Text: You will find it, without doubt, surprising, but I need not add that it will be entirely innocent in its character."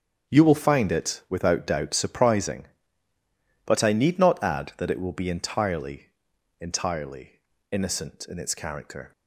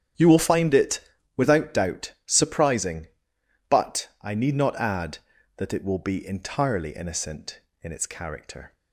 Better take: second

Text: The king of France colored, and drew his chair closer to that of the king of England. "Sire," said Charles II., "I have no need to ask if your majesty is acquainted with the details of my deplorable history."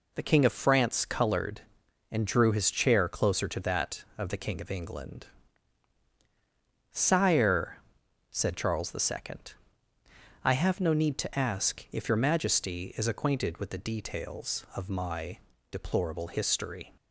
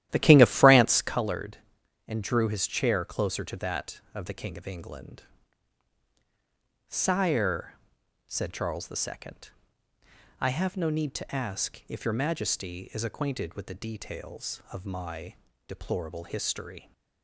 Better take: first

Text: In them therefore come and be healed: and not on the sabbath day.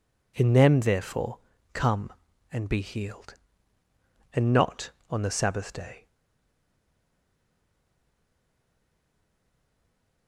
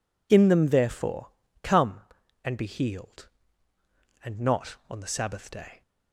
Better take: second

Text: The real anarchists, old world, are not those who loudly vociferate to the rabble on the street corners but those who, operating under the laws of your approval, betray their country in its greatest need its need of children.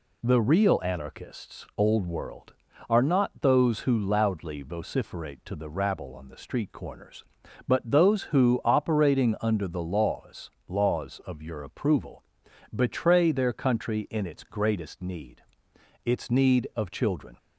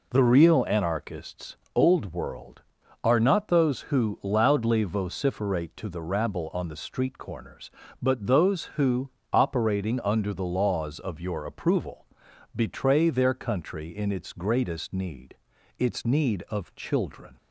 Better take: second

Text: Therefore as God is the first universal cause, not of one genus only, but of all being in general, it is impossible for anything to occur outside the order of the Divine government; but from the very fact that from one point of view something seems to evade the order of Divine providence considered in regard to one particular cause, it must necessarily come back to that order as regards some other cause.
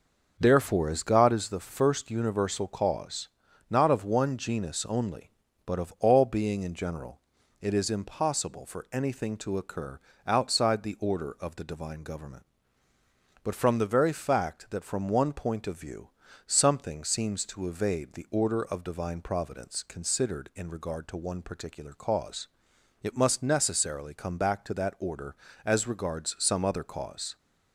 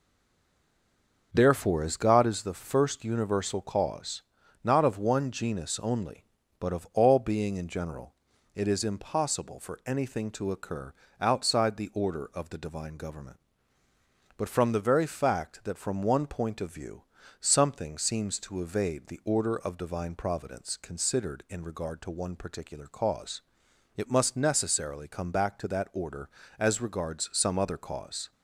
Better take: first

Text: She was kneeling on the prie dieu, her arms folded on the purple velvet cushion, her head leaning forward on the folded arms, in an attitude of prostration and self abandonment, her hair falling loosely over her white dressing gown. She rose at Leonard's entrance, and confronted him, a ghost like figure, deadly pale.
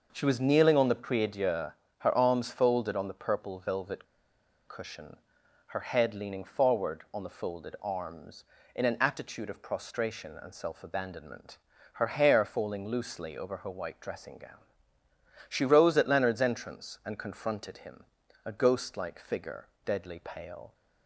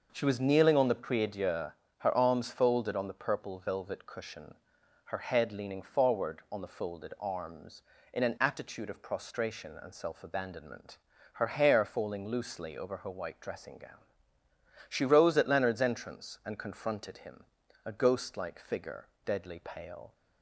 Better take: second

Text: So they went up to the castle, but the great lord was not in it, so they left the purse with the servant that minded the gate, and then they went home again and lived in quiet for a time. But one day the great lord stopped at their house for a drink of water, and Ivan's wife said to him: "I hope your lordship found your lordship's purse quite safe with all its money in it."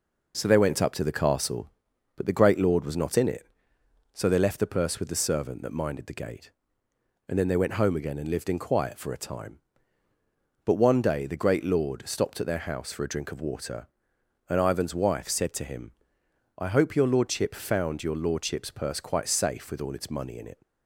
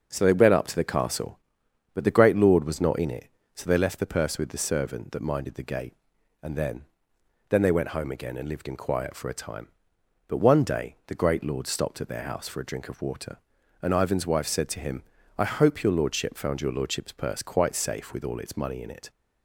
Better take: first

